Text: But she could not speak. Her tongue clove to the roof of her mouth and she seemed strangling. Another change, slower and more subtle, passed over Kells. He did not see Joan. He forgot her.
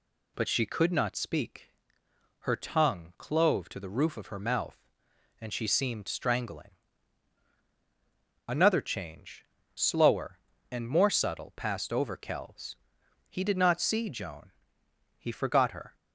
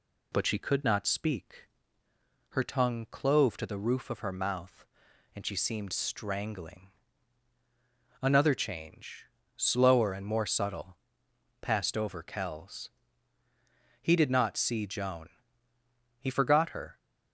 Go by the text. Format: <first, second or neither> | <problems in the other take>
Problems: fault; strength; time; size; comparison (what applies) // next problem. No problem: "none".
neither | none